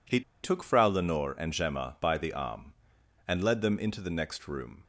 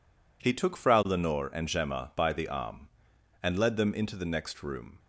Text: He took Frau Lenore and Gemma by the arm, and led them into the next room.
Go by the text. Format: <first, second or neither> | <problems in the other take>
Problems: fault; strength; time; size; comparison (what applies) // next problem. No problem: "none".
second | pauses between "He" and "took"; slight; at 0.2 s; 0.21 s long